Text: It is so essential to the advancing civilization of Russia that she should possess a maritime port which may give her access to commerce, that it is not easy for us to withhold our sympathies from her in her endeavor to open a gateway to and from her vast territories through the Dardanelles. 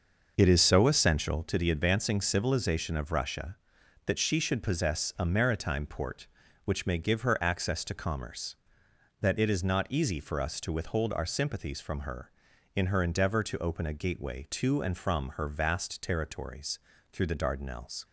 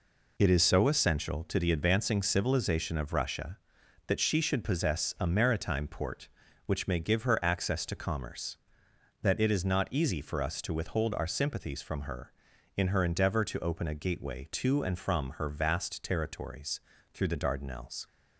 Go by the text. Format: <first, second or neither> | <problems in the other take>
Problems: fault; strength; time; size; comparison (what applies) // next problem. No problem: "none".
second | starts louder than the rest; noticeable; until 1.5 s; 6 dB // pauses between "territories" and "through"; slight; at 16.8 s; 0.32 s long; slight in the second